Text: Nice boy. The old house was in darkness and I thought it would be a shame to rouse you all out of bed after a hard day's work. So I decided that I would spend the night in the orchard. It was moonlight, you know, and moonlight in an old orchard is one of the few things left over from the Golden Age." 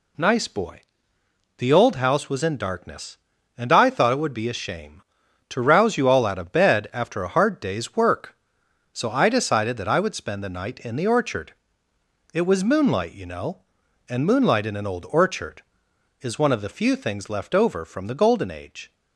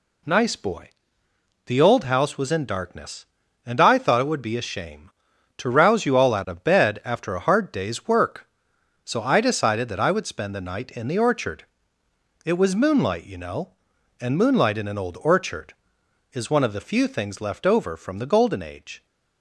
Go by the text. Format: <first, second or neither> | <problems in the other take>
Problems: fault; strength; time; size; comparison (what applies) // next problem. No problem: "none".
neither | none